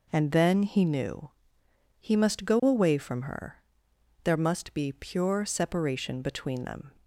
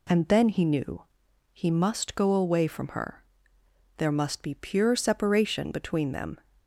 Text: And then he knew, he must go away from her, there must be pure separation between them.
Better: neither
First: none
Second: none

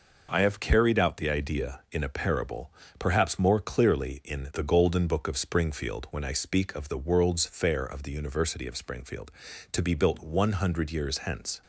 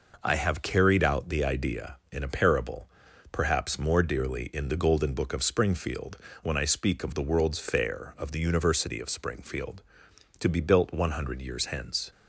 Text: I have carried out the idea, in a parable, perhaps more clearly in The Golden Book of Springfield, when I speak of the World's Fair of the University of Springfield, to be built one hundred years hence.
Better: first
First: none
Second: says "dearly" for "clearly"; at 4.0 s

